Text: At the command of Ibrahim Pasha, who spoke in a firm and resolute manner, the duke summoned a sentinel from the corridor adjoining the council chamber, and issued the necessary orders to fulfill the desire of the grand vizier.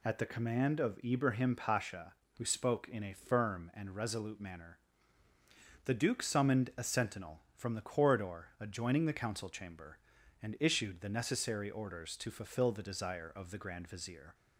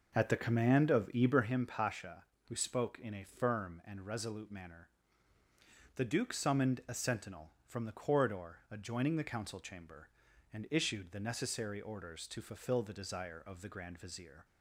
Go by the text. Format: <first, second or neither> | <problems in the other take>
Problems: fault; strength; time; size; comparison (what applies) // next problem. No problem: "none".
first | starts louder than the rest; noticeable; until 1.5 s; 5.5 dB